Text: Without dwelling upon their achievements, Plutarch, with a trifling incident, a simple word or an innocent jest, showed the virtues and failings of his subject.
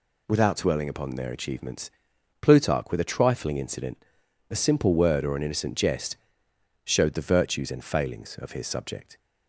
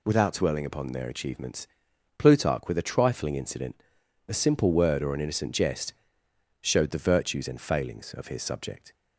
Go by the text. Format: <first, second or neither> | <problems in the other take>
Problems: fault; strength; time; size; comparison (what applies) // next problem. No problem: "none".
neither | none